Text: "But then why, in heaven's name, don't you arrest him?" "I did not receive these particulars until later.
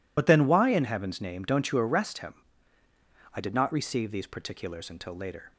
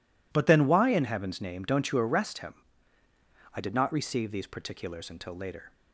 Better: second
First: loses the start of "But"; at 0.1 s; 55 ms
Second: none

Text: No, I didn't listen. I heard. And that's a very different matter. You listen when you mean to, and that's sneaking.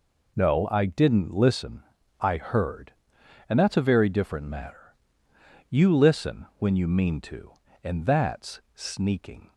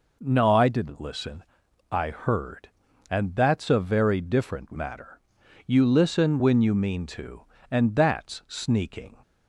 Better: neither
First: none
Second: none

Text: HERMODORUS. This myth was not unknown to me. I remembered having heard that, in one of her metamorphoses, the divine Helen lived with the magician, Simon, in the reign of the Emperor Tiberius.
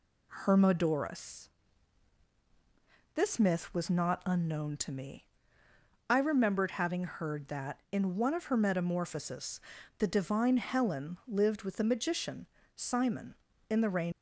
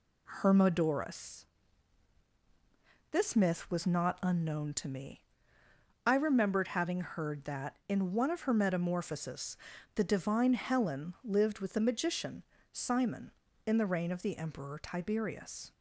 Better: second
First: stops before "of the Emperor Tiberius"; at 14.1 s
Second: none

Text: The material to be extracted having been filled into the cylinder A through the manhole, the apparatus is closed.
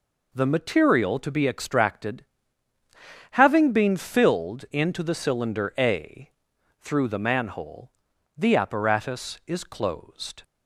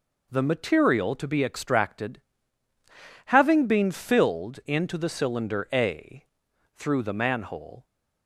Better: first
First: pauses between "extracted" and "having"; at 2.2 s; 1.0 s long // pauses between "A" and "through"; noticeable; at 6.2 s; 0.50 s long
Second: pauses between "extracted" and "having"; at 2.2 s; 1.0 s long // pauses between "A" and "through"; noticeable; at 6.2 s; 0.50 s long // stops before "the apparatus is closed"; at 7.8 s

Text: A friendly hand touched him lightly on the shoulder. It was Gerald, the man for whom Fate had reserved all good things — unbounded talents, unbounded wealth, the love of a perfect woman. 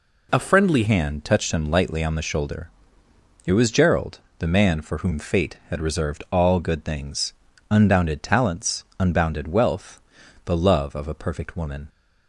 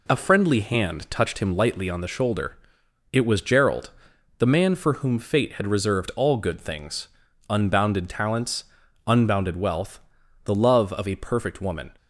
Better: second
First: changes voice at "hand"; from 0.8 s on; 11.0 s long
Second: none

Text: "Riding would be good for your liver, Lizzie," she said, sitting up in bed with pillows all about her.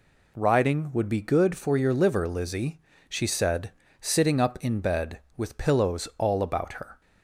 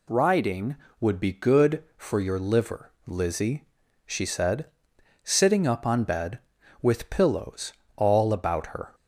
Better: first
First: none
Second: says "on" for "in"; at 5.8 s // pauses between "pillows" and "all"; slight; at 7.7 s; 0.20 s long

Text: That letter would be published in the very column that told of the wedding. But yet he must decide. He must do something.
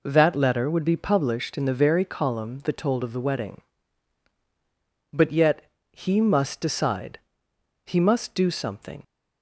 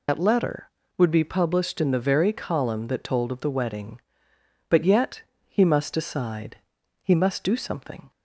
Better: first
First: pauses between "yet" and "he"; slight; at 5.6 s; 0.28 s long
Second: loses the start of "That"; at 0.0 s; 80 ms // pauses between "yet" and "he"; slight; at 5.2 s; 0.26 s long

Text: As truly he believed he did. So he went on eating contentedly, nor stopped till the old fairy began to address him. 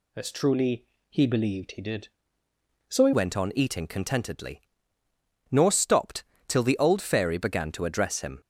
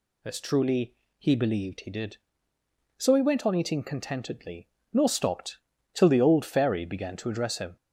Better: second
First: pauses between "truly" and "he"; slight; at 0.8 s; 0.24 s long // changes voice at "went"; from 3.1 s on; 5.3 s long // pauses between "stopped" and "till"; slight; at 6.2 s; 0.24 s long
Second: pauses between "truly" and "he"; slight; at 0.9 s; 0.24 s long // pauses between "stopped" and "till"; slight; at 5.5 s; 0.34 s long

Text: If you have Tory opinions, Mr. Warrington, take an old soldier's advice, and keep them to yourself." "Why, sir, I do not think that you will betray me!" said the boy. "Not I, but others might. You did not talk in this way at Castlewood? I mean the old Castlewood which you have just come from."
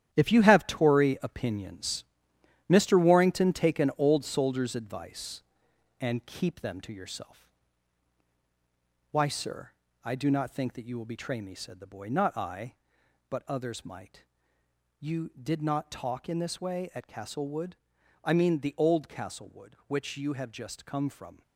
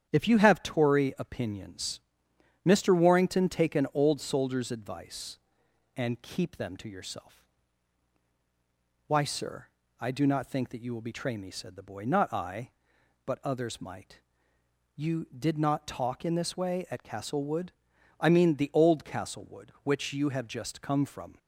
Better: second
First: gets quieter; strong; throughout; 9 dB // starts louder than the rest; strong; until 1.1 s; 10.5 dB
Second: starts louder than the rest; strong; until 1.1 s; 9 dB

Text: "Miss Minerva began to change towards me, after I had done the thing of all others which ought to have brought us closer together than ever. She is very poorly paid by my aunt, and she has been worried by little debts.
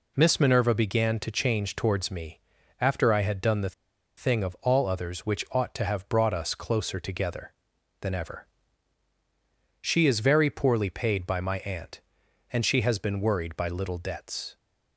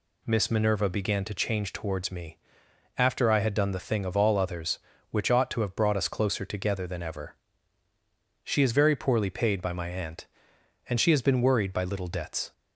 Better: second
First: pauses between "the" and "thing"; at 3.7 s; 0.44 s long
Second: none

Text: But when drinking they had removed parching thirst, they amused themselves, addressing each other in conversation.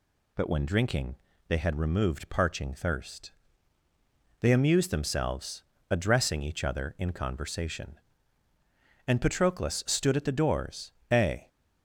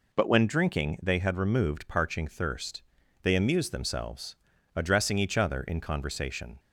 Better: second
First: pauses between "drinking" and "they"; slight; at 1.1 s; 0.32 s long // goes on to say "And Patroclus stood at the doors a"; strong; from 9.0 s on; 2.4 s long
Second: none

